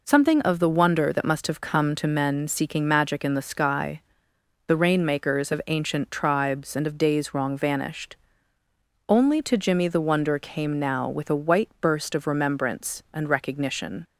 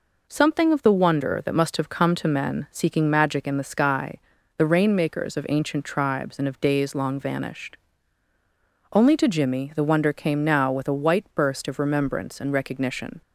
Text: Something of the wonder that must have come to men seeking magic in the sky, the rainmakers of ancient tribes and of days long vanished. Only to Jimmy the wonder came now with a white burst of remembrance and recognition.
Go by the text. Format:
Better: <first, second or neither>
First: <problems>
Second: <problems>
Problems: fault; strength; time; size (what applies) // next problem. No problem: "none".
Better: second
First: says "wrong" for "long"; at 7.3 s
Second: none